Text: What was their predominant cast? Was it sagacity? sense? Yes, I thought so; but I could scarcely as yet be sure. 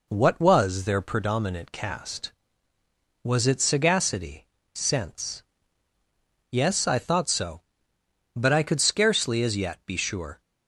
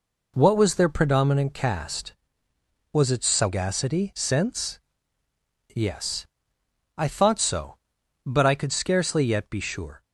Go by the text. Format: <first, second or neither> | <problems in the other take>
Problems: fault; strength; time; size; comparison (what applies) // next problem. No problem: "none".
first | skips "as"; at 9.2 s